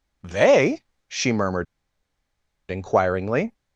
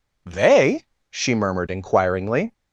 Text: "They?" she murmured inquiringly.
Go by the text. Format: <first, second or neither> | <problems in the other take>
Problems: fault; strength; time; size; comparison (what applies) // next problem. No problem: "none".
second | pauses between "murmured" and "inquiringly"; at 1.6 s; 1.0 s long